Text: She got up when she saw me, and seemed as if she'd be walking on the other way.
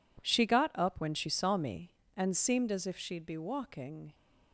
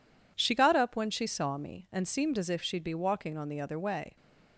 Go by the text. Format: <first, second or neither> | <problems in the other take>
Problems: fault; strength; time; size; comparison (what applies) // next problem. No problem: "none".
second | stops before "on the other way"; at 4.1 s